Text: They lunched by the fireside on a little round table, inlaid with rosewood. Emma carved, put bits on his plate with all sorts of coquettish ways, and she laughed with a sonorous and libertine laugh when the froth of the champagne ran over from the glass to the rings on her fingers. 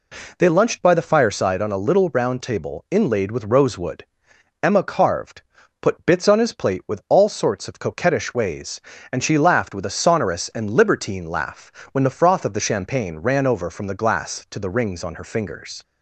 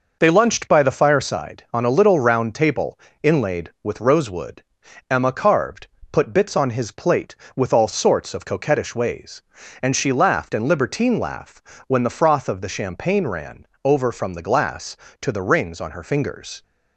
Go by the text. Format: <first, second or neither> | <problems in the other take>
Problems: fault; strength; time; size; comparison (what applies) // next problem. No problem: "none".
first | skips "with a sonorous"; at 10.5 s // pauses between "laugh" and "when"; slight; at 11.6 s; 0.28 s long; slight in the first // pauses between "ran" and "over"; slight; at 13.6 s; 0.16 s long